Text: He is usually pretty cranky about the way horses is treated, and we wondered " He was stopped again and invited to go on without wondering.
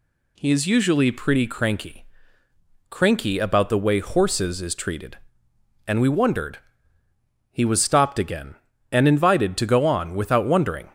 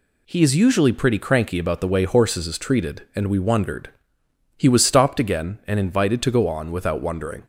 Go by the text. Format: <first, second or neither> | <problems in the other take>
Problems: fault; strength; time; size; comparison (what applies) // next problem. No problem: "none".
second | says "cranky" twice; at 2.8 s